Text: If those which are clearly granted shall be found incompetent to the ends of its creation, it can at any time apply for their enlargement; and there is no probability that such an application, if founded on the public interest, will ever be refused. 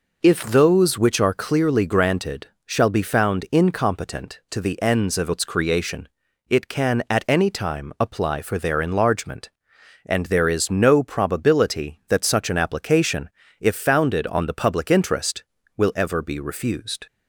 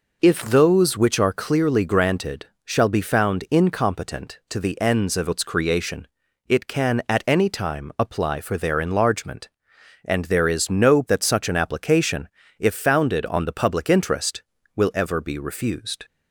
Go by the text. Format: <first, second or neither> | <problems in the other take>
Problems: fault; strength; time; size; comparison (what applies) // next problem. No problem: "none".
first | pauses between "granted" and "shall"; slight; at 2.4 s; 0.20 s long; slight in the first // skips "probability"; at 11.0 s